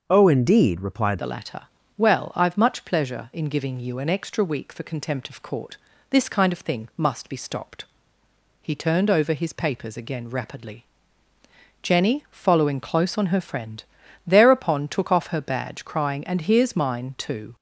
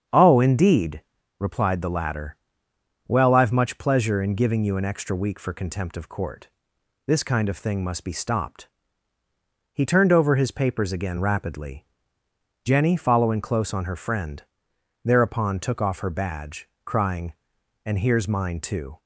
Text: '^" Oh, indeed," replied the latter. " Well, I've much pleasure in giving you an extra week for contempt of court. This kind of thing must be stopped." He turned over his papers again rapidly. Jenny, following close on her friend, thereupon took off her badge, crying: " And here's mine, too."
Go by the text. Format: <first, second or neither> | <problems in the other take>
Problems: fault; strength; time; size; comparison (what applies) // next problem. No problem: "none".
second | starts louder than the rest; until 1.0 s; 6.5 dB; strong in the second // changes voice at "the"; from 1.1 s on; 16.4 s long